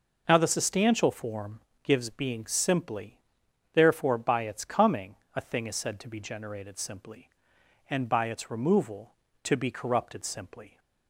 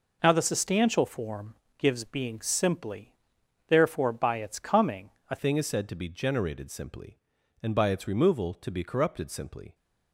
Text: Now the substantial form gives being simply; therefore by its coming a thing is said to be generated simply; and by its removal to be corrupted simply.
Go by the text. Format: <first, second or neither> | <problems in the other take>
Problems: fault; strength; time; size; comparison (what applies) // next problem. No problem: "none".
first | pauses between "form" and "gives"; slight; at 1.5 s; 0.22 s long; slight in the first // pauses between "coming" and "a"; slight; at 5.1 s; 0.20 s long; slight in the first // changes voice at "thing"; from 5.3 s on; 4.4 s long